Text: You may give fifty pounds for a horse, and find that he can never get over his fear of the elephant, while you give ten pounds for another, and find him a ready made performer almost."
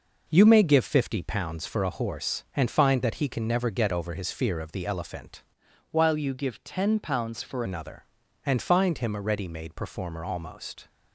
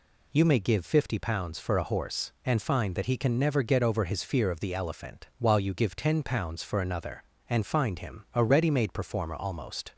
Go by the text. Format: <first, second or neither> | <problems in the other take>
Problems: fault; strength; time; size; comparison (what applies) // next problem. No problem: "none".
second | changes voice from "while" to "for"; from 5.8 to 7.6 s; 1.8 s long